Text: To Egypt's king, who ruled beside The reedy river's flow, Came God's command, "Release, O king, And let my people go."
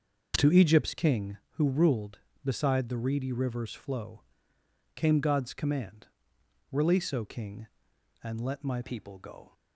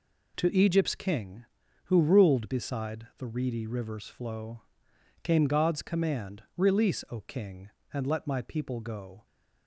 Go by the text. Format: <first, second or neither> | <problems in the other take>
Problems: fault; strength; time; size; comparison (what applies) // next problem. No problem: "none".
second | starts louder than the rest; noticeable; until 1.3 s; 6 dB // changes voice at "people"; from 8.8 s on; 0.7 s long